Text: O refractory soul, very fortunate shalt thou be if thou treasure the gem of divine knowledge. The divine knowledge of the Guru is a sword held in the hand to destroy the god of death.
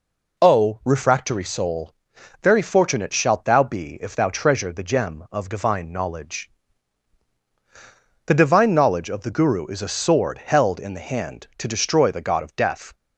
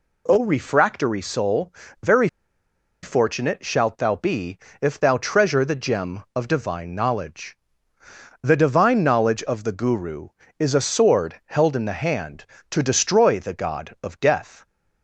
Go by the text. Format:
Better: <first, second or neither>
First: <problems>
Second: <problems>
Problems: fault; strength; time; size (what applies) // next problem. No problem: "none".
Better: first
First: none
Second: pauses between "very" and "fortunate"; noticeable; at 2.2 s; 0.76 s long // pauses between "be" and "if"; slight; at 4.5 s; 0.24 s long